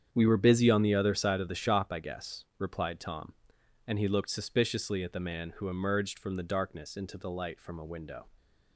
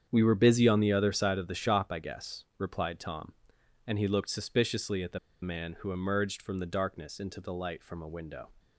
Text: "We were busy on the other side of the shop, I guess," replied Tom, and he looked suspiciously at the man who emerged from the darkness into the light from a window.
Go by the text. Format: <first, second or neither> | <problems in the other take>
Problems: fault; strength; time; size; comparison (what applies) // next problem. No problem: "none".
first | starts louder than the rest; strong; until 1.1 s; 8 dB; strong in the first // pauses between "the" and "man"; slight; at 5.1 s; 0.24 s long